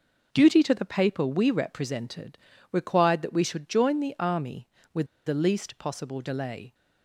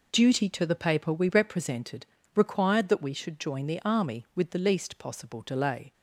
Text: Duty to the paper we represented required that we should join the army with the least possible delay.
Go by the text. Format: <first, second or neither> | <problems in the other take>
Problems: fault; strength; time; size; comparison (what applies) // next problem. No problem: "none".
second | pauses between "represented" and "required"; slight; at 2.3 s; 0.32 s long; slight in the second // pauses between "with" and "the"; slight; at 5.0 s; 0.19 s long